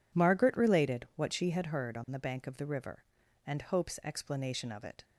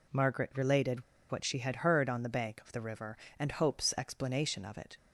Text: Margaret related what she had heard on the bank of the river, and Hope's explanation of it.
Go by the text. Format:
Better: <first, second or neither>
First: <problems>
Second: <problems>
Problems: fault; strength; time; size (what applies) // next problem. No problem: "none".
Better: first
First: none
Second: pauses between "related" and "what"; slight; at 1.0 s; 0.27 s long